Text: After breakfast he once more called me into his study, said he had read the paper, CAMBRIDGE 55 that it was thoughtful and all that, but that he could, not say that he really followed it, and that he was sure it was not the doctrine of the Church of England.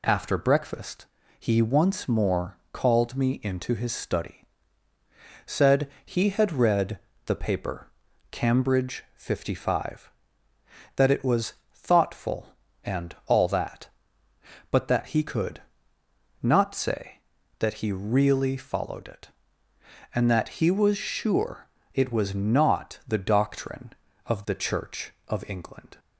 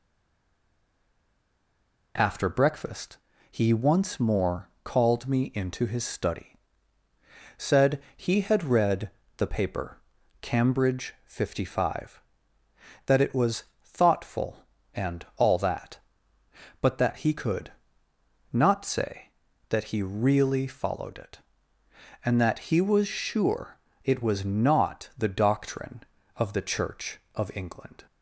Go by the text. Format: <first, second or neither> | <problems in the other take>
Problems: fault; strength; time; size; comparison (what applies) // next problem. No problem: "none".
first | stays silent before the first word; until 2.1 s; 2.1 s long // pauses between "breakfast" and "he"; slight; at 3.1 s; 0.32 s long; slight in the first // pauses between "said" and "he"; slight; at 8.0 s; 0.16 s long; slight in the first // pauses between "read" and "the"; slight; at 9.1 s; 0.26 s long; slight in the first // pauses between "was" and "thoughtful"; slight; at 13.6 s; 0.18 s long; slight in the first // pauses between "sure" and "it"; slight; at 23.7 s; 0.28 s long; slight in the first